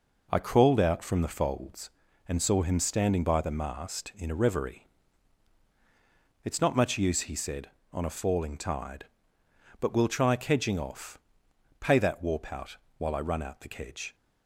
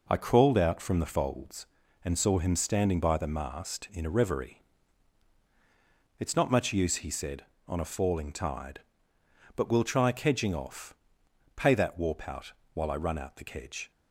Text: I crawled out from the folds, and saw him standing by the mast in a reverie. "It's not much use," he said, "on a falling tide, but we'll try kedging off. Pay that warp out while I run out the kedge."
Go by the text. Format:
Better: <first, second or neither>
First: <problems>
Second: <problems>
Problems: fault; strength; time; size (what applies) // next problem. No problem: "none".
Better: neither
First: pauses between "out" and "while"; slight; at 12.7 s; 0.22 s long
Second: pauses between "out" and "while"; slight; at 12.5 s; 0.22 s long